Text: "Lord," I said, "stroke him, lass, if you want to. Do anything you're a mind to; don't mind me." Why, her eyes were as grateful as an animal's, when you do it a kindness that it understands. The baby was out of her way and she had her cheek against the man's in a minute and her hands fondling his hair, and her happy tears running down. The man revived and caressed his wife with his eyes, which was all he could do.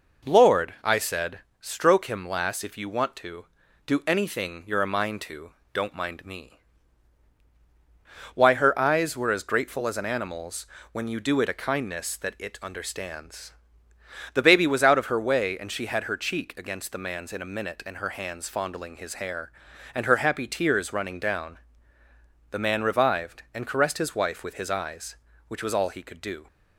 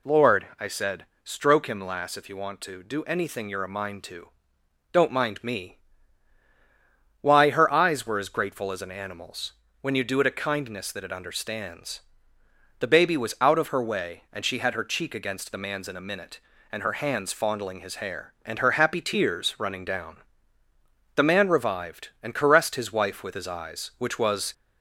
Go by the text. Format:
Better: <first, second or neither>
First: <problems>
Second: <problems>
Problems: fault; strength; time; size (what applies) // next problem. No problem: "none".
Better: first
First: none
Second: stops before "all he could do"; at 24.5 s